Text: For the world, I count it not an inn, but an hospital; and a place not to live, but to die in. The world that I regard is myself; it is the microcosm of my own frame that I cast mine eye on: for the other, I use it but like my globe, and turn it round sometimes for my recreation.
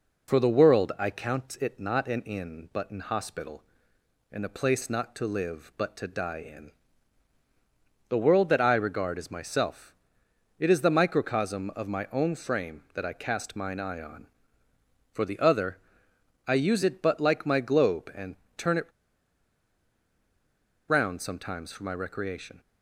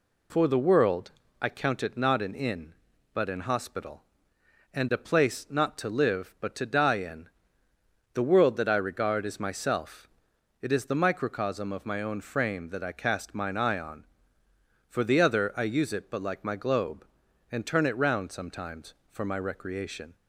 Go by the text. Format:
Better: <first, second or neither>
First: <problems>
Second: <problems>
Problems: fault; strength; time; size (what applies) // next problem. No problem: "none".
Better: second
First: pauses between "and" and "turn"; slight; at 18.3 s; 0.20 s long // pauses between "it" and "round"; strong; at 18.8 s; 2.0 s long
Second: none